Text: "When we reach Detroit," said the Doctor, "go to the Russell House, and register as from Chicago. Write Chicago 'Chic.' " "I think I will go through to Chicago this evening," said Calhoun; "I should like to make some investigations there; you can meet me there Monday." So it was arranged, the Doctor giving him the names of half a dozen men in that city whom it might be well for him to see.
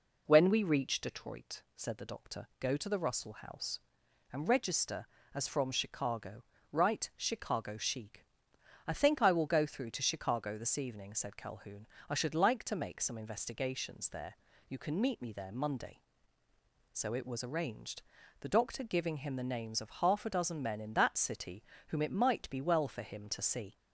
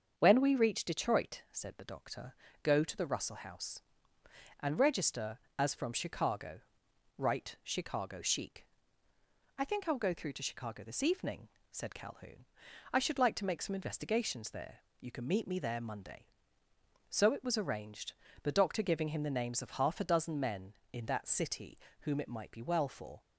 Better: first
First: pauses between "city" and "whom"; slight; at 21.6 s; 0.26 s long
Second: starts louder than the rest; strong; until 1.1 s; 7 dB // pauses between "city" and "whom"; slight; at 21.7 s; 0.22 s long // stops before "him to see"; at 23.1 s

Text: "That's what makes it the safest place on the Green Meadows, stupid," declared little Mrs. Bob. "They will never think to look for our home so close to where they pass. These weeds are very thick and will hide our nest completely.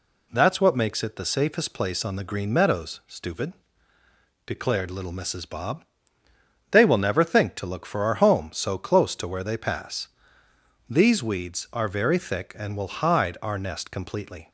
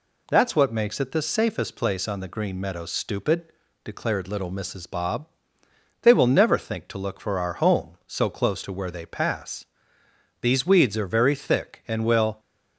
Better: first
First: none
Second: stops before "hide our nest completely"; at 12.3 s

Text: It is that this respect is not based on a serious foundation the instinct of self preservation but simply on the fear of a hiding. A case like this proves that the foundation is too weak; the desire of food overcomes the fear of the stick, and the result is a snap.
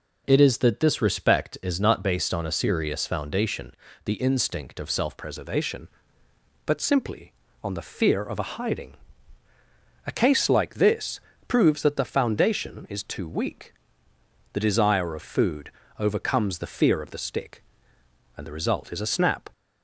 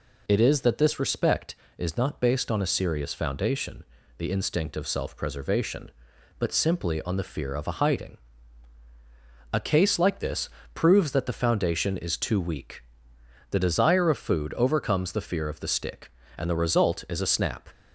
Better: second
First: pauses between "foundation" and "the"; slight; at 3.7 s; 0.32 s long // changes voice at "preservation"; from 5.1 s on; 14.3 s long // pauses between "this" and "proves"; slight; at 11.1 s; 0.28 s long // pauses between "food" and "overcomes"; slight; at 15.6 s; 0.30 s long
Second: pauses between "foundation" and "the"; slight; at 3.8 s; 0.34 s long // pauses between "this" and "proves"; slight; at 10.4 s; 0.24 s long

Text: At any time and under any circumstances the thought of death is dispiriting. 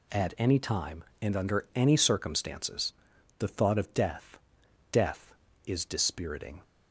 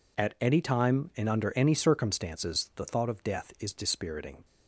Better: second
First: pauses between "circumstances" and "the"; noticeable; at 2.9 s; 0.48 s long // says "death" twice; at 4.9 s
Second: none

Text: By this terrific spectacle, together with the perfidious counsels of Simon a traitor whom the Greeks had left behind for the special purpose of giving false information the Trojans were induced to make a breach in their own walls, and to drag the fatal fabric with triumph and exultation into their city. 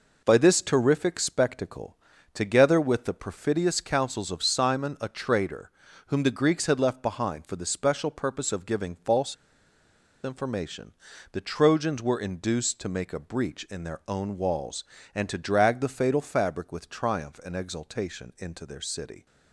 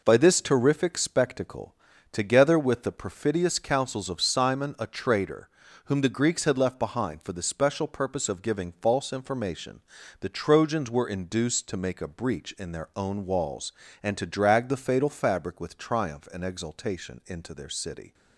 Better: second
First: pauses between "traitor" and "whom"; at 5.6 s; 0.38 s long // pauses between "false" and "information"; noticeable; at 9.3 s; 0.88 s long // pauses between "information" and "the"; at 10.9 s; 0.40 s long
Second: pauses between "traitor" and "whom"; at 5.4 s; 0.38 s long // pauses between "information" and "the"; at 9.8 s; 0.40 s long

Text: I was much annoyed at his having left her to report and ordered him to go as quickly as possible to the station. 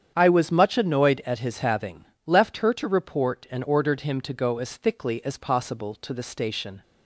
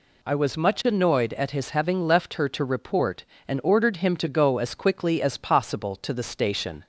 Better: second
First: starts louder than the rest; strong; until 1.1 s; 8.5 dB // pauses between "having" and "left"; slight; at 2.0 s; 0.22 s long // says "thickly" for "quickly"; at 4.7 s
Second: none

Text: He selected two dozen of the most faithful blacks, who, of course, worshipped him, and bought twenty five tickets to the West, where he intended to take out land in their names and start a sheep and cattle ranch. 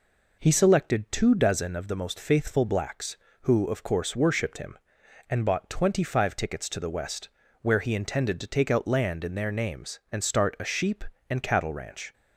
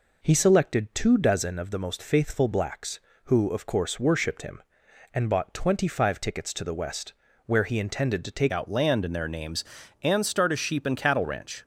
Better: first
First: none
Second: changes voice at "out"; from 8.5 s on; 3.1 s long

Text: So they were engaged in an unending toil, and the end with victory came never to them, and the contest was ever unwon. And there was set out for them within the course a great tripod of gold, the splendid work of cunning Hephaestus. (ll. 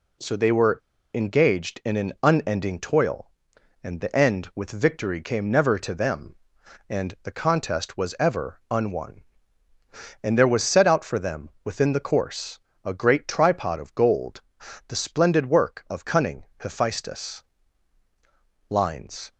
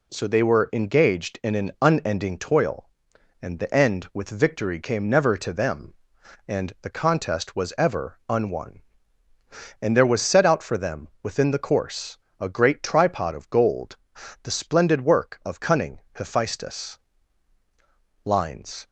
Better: second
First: pauses between "were" and "engaged"; at 0.7 s; 0.36 s long // pauses between "them" and "within"; slight; at 11.4 s; 0.16 s long // pauses between "course" and "a"; slight; at 12.5 s; 0.26 s long // pauses between "cunning" and "Hephaestus"; slight; at 16.4 s; 0.16 s long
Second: pauses between "them" and "within"; slight; at 11.0 s; 0.16 s long // pauses between "course" and "a"; slight; at 12.1 s; 0.22 s long // pauses between "cunning" and "Hephaestus"; slight; at 15.9 s; 0.16 s long

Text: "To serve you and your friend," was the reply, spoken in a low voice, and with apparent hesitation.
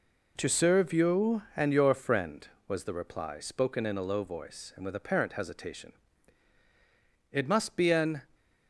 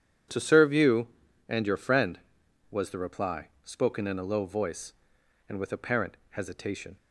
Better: second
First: goes on to say "It must be an"; noticeable; from 7.3 s on; 0.86 s long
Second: none

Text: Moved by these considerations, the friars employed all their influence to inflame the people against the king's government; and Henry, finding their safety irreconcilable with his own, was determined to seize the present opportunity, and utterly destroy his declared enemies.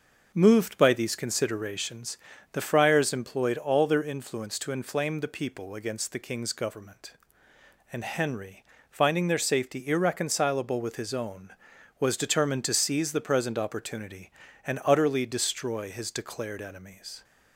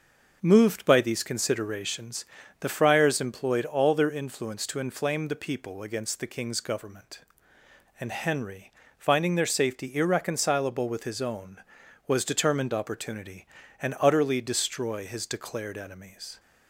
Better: first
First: none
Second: skips "to seize the present"; at 12.7 s

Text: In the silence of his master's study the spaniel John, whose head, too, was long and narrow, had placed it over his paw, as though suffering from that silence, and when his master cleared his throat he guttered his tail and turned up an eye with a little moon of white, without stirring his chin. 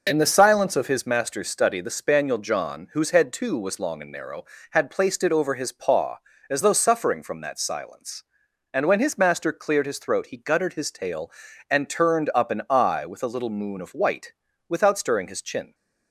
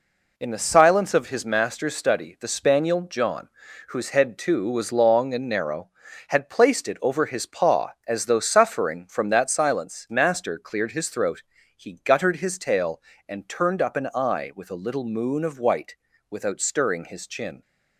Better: first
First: none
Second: skips "and when his"; at 10.0 s // pauses between "throat" and "he"; slight; at 11.4 s; 0.34 s long

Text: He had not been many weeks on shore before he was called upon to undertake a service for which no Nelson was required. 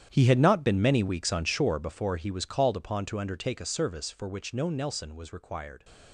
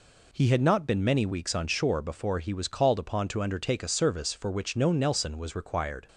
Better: second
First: gets quieter; strong; throughout; 14.5 dB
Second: none

